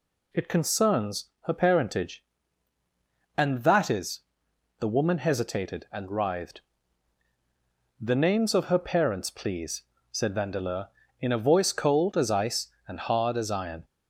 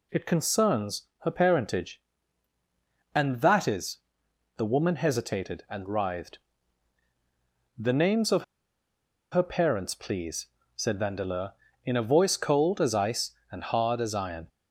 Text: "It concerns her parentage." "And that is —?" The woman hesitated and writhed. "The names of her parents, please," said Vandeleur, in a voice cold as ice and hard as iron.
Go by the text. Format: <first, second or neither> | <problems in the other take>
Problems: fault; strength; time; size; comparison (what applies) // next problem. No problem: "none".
first | pauses between "concerns" and "her"; slight; at 1.0 s; 0.16 s long; slight in the first // pauses between "of" and "her"; noticeable; at 8.4 s; 0.87 s long